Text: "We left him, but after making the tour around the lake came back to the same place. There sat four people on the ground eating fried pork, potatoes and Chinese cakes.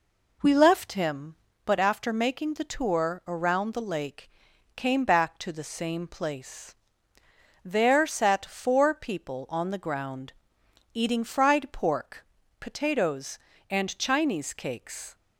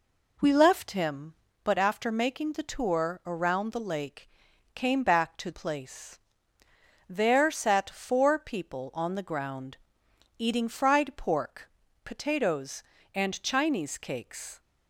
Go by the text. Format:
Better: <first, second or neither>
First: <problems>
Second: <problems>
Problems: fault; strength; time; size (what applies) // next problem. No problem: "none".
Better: first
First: pauses between "lake" and "came"; noticeable; at 4.2 s; 0.46 s long // pauses between "ground" and "eating"; noticeable; at 10.3 s; 0.60 s long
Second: pauses between "lake" and "came"; noticeable; at 4.2 s; 0.46 s long // skips "the same"; at 5.5 s // pauses between "ground" and "eating"; noticeable; at 9.7 s; 0.60 s long